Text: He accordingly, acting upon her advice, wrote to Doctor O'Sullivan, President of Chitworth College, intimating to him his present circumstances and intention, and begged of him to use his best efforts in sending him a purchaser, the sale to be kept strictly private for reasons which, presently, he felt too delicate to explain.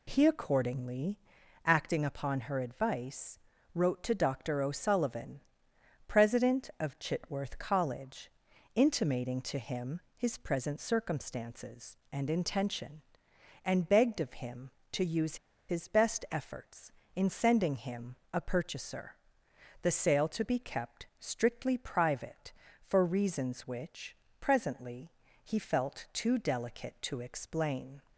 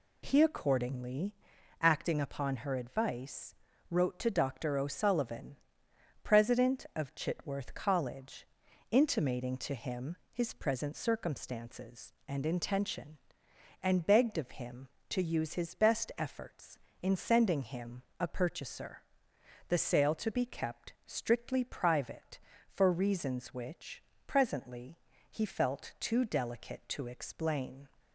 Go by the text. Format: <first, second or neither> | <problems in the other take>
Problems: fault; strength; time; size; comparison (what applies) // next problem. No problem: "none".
second | pauses between "him" and "his"; slight; at 10.0 s; 0.16 s long; slight in the second // pauses between "use" and "his"; slight; at 15.3 s; 0.32 s long // pauses between "him" and "a"; slight; at 18.1 s; 0.16 s long; slight in the second